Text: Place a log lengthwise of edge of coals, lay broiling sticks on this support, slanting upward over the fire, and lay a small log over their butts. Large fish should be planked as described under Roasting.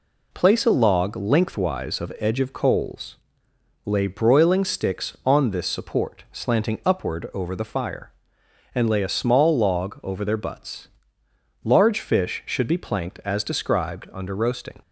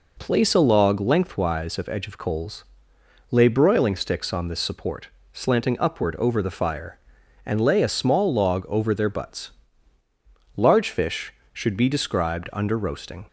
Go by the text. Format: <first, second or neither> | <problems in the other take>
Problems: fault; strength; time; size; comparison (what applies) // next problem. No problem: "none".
first | skips "planked as"; at 11.8 s